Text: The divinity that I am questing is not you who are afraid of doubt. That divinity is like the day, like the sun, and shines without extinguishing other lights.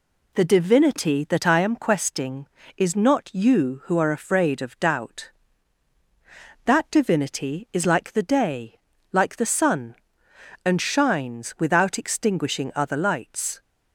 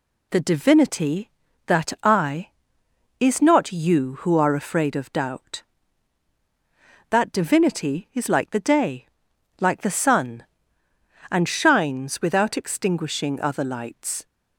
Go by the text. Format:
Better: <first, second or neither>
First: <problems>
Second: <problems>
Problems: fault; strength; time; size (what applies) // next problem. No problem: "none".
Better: first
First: none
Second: skips "am questing"; at 2.8 s